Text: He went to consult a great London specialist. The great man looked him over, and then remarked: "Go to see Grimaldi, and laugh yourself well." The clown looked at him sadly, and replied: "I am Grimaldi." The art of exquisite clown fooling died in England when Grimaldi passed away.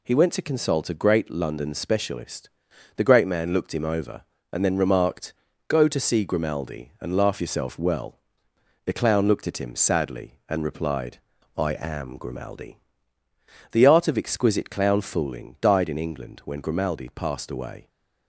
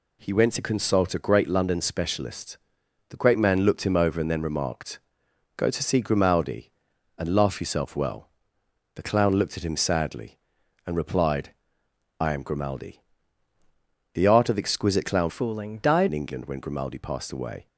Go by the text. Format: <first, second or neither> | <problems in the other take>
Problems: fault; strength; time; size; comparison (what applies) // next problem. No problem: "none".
first | changes voice from "fooling" to "died"; from 15.2 to 16.0 s; 0.8 s long